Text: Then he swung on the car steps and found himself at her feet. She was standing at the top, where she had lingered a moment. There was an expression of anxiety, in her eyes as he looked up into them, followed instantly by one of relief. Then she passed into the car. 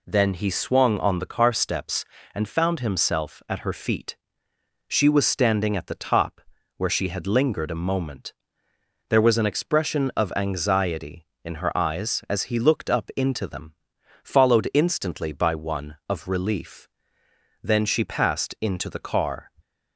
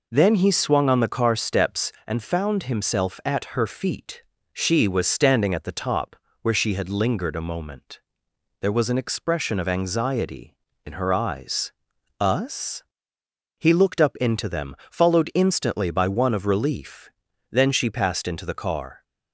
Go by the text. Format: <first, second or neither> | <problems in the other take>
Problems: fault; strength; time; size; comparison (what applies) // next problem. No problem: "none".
first | says "us" for "as"; at 12.1 s